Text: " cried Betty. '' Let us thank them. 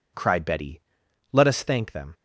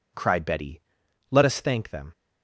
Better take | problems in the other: neither | none

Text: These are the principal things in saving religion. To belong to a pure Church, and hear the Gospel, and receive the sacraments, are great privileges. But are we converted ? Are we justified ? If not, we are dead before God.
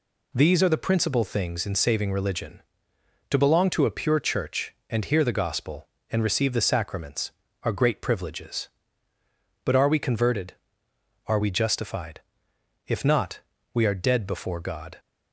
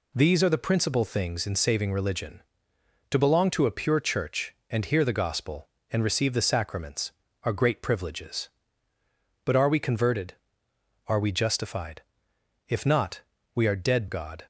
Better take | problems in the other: first | skips "before"; at 14.0 s

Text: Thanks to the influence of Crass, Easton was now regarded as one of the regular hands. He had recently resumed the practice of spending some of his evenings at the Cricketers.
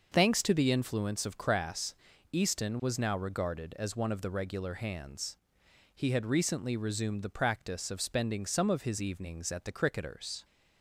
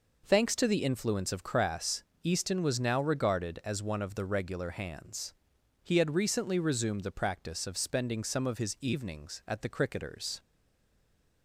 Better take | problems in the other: first | stays silent after the last word; from 10.3 s on; 1.1 s long

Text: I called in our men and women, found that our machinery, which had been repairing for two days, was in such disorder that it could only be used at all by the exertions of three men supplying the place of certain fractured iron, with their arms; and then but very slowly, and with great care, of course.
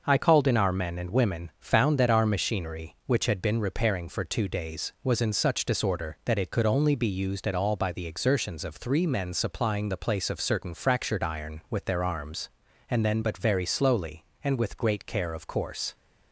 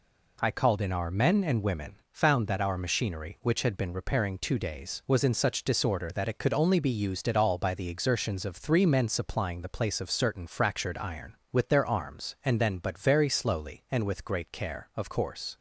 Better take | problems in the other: first | skips "for"; at 4.3 s

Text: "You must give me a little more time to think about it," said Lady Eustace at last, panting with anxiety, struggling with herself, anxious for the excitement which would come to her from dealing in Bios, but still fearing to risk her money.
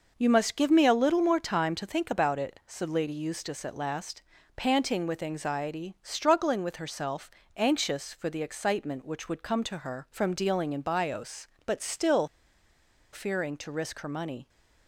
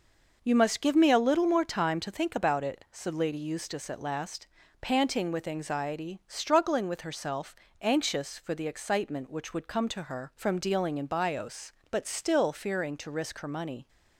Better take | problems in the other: second | pauses between "still" and "fearing"; noticeable; at 12.2 s; 0.84 s long

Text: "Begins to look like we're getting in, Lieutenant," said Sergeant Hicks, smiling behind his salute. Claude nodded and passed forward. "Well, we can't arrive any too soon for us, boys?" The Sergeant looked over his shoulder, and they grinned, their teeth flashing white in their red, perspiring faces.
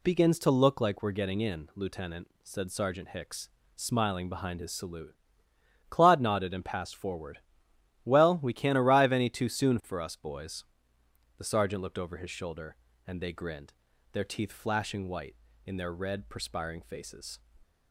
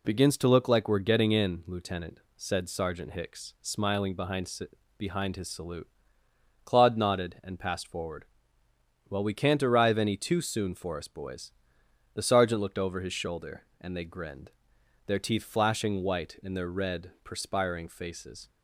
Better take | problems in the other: first | says "behind" twice; at 4.9 s

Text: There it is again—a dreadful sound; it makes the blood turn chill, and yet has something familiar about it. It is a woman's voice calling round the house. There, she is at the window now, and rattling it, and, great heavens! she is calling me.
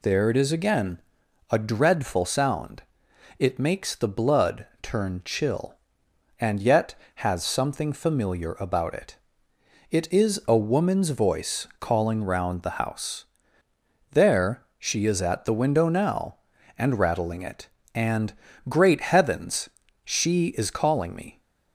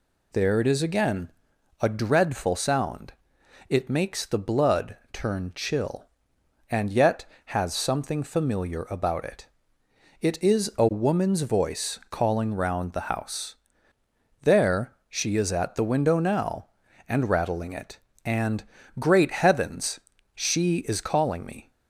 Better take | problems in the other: neither | pauses between "blood" and "turn"; slight; the same in both

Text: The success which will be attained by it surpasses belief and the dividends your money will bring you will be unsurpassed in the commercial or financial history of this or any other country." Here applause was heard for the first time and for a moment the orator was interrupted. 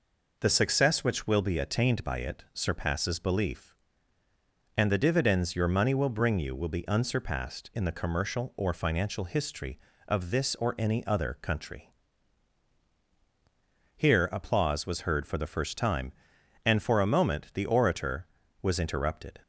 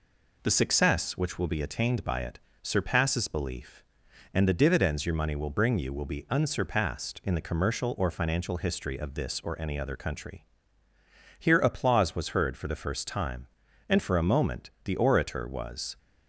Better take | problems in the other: first | pauses between "it" and "surpasses"; slight; at 2.3 s; 0.22 s long // pauses between "moment" and "the"; slight; at 14.6 s; 0.16 s long // stops before "interrupted"; at 15.9 s

